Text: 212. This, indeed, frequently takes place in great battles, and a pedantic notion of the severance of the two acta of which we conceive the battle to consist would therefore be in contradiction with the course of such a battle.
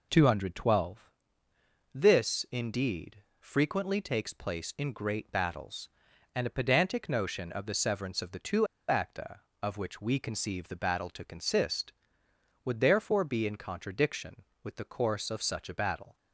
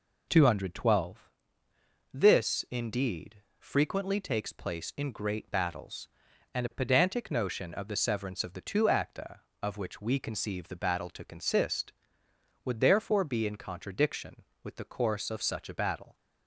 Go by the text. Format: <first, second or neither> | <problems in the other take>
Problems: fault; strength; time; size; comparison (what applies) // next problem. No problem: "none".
second | pauses between "two" and "acta"; slight; at 8.6 s; 0.23 s long